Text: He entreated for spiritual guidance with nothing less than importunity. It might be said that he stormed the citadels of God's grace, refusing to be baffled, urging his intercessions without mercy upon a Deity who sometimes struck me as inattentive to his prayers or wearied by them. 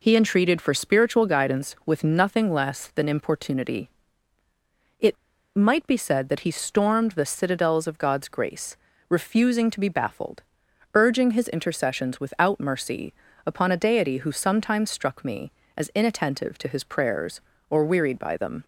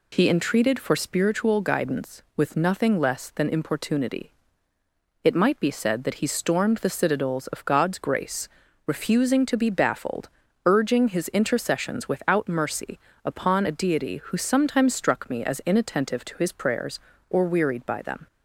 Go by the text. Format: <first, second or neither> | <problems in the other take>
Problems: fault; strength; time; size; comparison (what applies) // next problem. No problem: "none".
second | pauses between "It" and "might"; at 5.1 s; 0.40 s long // pauses between "mercy" and "upon"; slight; at 13.1 s; 0.32 s long; slight in the second